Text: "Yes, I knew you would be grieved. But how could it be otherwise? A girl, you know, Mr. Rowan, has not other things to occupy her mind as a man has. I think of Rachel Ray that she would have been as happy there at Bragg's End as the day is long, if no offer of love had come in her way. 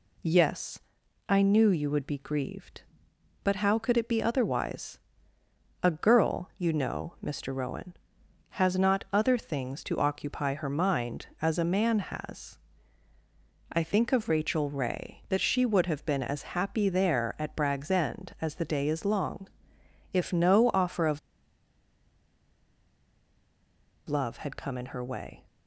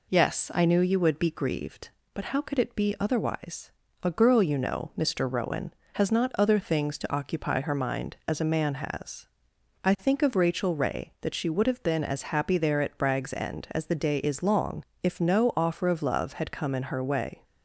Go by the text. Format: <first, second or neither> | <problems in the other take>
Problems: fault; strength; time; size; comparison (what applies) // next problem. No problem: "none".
second | pauses between "of" and "love"; strong; at 21.1 s; 2.8 s long